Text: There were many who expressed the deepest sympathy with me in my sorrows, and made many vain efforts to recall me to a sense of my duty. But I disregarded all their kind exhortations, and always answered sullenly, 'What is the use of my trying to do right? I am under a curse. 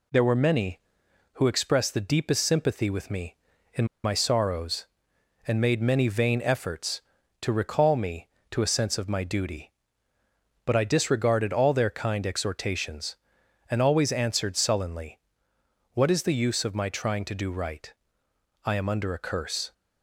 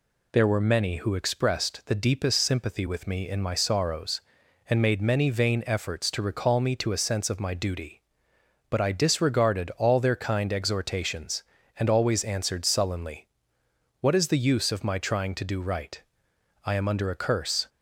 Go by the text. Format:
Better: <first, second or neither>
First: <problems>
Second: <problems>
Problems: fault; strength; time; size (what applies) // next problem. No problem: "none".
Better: second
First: pauses between "in" and "my"; slight; at 3.8 s; 0.19 s long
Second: none